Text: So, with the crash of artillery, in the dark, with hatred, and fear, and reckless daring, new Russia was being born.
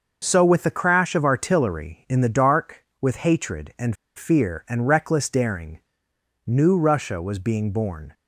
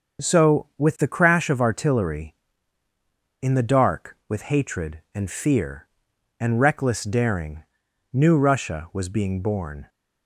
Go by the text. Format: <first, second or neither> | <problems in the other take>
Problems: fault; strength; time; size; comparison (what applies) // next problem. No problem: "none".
second | starts louder than the rest; until 1.2 s; 6 dB; also in the second // pauses between "and" and "fear"; slight; at 3.9 s; 0.23 s long